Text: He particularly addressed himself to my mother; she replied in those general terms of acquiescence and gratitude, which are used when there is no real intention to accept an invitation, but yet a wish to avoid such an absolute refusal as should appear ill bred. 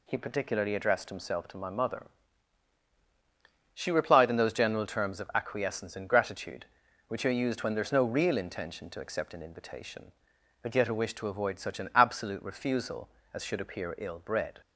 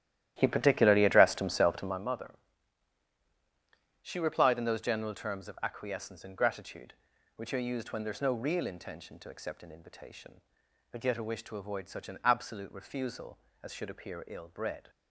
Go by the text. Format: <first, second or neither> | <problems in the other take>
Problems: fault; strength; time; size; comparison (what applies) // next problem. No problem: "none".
first | starts louder than the rest; strong; until 2.1 s; 12.5 dB